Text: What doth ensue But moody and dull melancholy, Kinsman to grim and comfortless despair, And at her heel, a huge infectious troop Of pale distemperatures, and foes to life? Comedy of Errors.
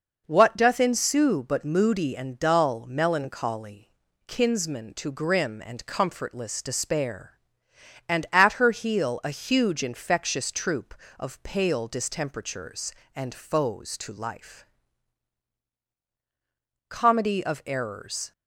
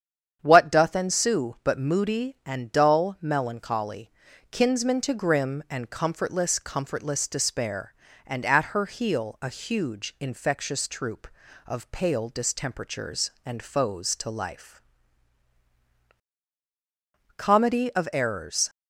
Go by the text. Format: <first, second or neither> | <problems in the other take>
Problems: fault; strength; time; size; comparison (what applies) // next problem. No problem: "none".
first | starts louder than the rest; strong; until 1.4 s; 8.5 dB // says "comfortless" twice; at 6.5 s